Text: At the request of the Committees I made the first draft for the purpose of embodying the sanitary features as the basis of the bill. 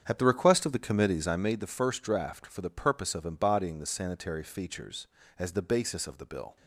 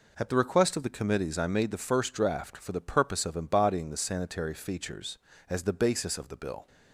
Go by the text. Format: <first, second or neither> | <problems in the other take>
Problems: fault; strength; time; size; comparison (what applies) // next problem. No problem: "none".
second | starts louder than the rest; strong; until 1.5 s; 8 dB